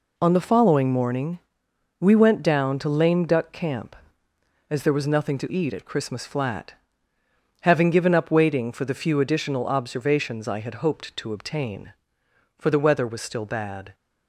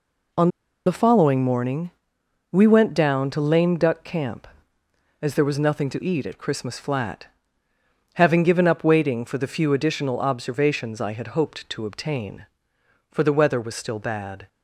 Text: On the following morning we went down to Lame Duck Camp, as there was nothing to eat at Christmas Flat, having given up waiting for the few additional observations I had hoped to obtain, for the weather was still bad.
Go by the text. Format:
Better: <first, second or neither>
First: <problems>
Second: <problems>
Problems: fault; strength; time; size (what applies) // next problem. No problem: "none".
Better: first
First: pauses between "morning" and "we"; noticeable; at 1.4 s; 0.60 s long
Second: pauses between "On" and "the"; at 0.4 s; 0.37 s long // pauses between "morning" and "we"; noticeable; at 1.9 s; 0.60 s long